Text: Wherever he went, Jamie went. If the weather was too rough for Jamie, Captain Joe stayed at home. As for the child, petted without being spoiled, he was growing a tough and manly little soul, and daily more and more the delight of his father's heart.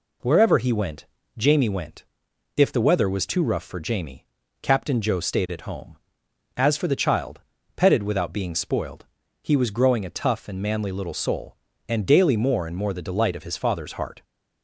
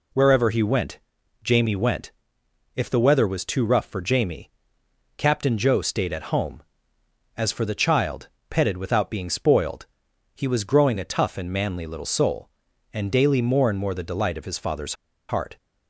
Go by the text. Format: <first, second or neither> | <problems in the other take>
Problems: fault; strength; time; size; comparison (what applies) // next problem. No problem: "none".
first | pauses between "father's" and "heart"; slight; at 14.9 s; 0.34 s long